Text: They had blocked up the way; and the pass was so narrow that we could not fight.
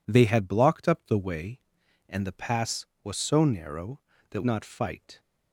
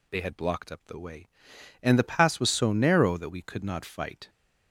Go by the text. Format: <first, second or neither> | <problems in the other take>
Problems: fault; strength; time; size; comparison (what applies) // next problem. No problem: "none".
second | skips "we could"; at 4.4 s